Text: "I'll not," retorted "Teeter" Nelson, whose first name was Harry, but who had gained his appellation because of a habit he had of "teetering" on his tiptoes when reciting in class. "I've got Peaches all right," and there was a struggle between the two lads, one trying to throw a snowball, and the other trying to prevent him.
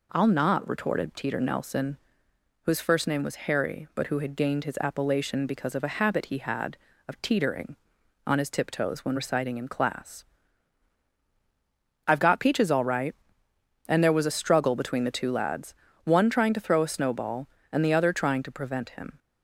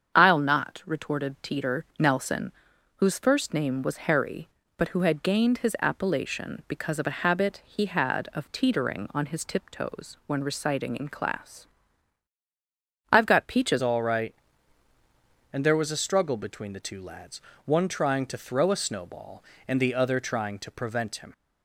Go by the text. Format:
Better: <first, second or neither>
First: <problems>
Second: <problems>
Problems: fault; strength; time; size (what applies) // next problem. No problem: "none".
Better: first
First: none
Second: starts louder than the rest; strong; until 1.1 s; 7.5 dB // changes voice at "all"; from 13.8 s on; 7.5 s long